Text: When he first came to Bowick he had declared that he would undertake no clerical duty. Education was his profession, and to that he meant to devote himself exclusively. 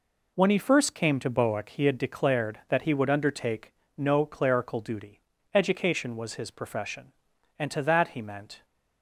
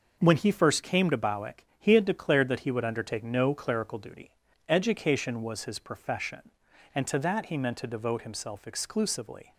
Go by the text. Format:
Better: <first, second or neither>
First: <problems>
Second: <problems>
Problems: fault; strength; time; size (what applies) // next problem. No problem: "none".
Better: second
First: pauses between "undertake" and "no"; slight; at 3.7 s; 0.24 s long // stops before "to devote himself exclusively"; at 8.6 s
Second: none